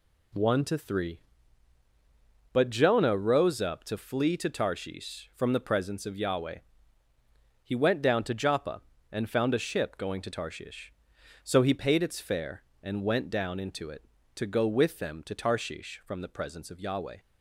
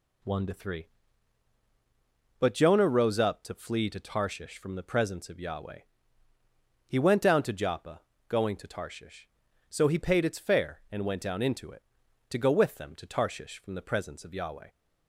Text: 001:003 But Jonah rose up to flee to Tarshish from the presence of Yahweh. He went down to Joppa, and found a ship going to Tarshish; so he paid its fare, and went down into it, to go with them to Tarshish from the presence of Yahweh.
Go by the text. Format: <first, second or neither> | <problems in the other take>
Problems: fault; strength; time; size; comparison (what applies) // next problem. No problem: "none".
first | skips "and found a ship"; at 8.1 s